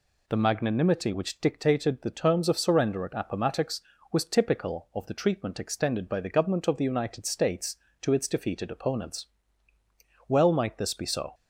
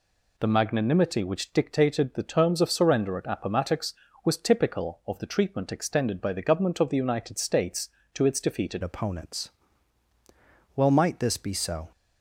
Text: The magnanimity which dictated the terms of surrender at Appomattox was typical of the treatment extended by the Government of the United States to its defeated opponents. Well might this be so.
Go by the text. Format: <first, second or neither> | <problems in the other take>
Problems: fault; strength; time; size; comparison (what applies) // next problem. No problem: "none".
first | changes voice at "opponents"; from 8.8 s on; 3.1 s long